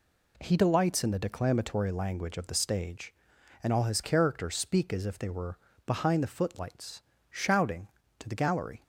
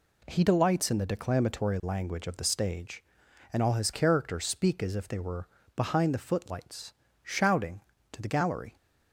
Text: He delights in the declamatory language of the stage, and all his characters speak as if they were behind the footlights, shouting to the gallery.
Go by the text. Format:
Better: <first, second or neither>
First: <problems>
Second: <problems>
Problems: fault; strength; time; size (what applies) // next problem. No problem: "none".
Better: neither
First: pauses between "were" and "behind"; slight; at 5.5 s; 0.28 s long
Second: pauses between "were" and "behind"; slight; at 5.4 s; 0.28 s long